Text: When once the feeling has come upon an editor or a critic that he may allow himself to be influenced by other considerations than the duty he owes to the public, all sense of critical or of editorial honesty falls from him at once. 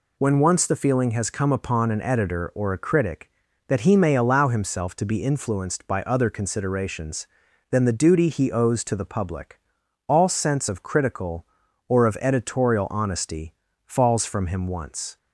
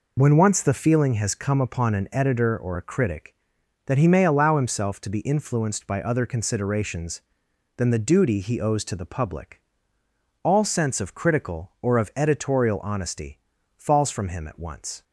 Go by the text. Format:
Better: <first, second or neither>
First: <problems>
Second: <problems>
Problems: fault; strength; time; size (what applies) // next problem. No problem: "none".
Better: second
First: pauses between "honesty" and "falls"; slight; at 13.5 s; 0.30 s long // skips "at"; at 14.6 s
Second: pauses between "honesty" and "falls"; at 13.3 s; 0.38 s long